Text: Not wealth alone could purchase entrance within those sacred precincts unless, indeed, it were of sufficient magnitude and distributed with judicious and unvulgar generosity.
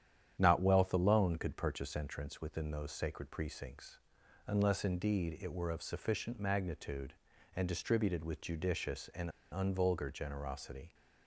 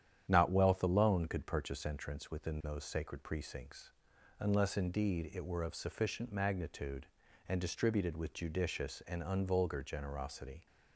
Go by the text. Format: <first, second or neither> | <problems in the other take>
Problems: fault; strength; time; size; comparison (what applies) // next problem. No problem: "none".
second | starts louder than the rest; strong; until 1.3 s; 9.5 dB; strong in the second // pauses between "precincts" and "unless"; noticeable; at 3.9 s; 0.46 s long; noticeable in the second // pauses between "and" and "unvulgar"; slight; at 9.2 s; 0.22 s long